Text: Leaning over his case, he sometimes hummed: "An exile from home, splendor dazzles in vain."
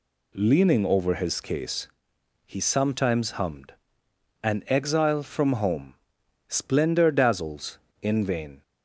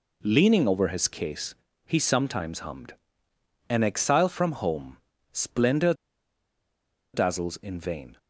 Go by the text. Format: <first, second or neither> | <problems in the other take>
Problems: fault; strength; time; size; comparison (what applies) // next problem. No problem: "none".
first | pauses between "splendor" and "dazzles"; at 5.9 s; 1.2 s long